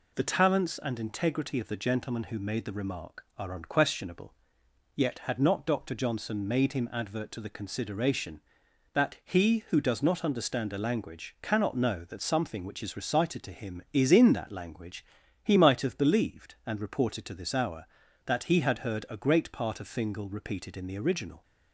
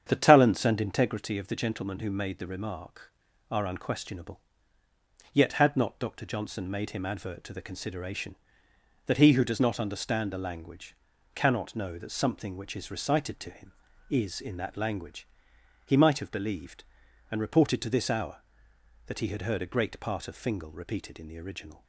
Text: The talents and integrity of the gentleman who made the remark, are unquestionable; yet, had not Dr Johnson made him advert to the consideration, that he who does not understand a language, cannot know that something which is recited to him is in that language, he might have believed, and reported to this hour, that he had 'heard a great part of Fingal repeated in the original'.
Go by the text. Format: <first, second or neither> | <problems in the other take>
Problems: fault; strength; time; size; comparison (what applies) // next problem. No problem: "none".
first | starts louder than the rest; strong; until 1.2 s; 8 dB